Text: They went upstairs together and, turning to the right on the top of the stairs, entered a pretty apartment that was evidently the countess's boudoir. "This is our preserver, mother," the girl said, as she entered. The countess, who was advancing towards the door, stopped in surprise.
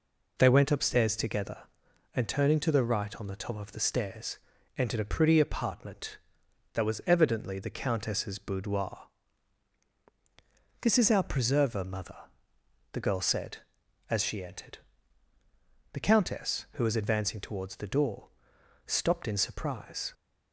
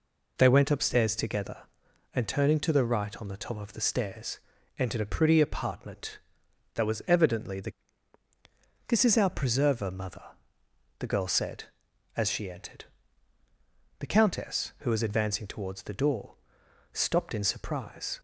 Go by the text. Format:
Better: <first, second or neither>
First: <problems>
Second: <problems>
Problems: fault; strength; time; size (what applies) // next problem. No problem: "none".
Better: first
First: none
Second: skips "countess's boudoir"; at 8.2 s